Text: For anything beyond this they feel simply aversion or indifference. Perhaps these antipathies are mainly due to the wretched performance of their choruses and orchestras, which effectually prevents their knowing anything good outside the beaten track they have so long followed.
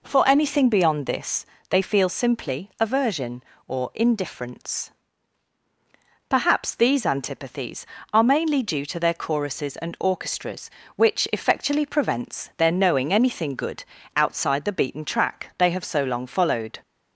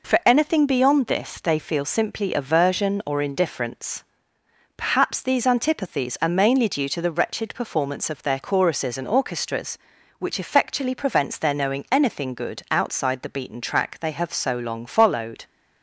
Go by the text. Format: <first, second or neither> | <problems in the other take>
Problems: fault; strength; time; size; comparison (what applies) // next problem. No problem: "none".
second | pauses between "this" and "they"; slight; at 1.4 s; 0.24 s long // skips "the wretched performance of"; at 8.9 s // pauses between "good" and "outside"; slight; at 13.8 s; 0.32 s long